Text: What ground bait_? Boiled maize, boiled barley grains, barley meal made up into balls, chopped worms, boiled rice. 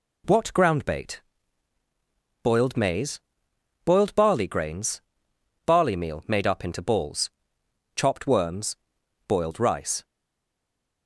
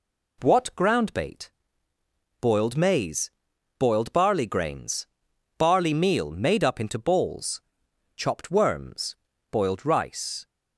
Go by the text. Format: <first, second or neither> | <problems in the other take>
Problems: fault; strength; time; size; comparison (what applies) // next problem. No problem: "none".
second | stays silent after the last word; from 10.0 s on; 1.0 s long